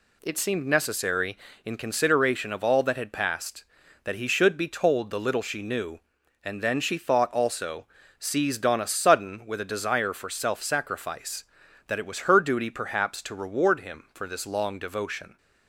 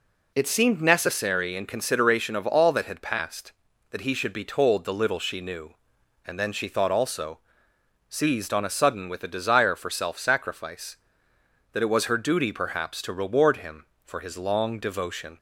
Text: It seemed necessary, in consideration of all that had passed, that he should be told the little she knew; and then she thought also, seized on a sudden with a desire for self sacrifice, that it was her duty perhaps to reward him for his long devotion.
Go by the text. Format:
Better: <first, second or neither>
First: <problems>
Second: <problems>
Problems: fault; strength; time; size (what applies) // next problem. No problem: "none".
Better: second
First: says "this" for "his"; at 14.2 s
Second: none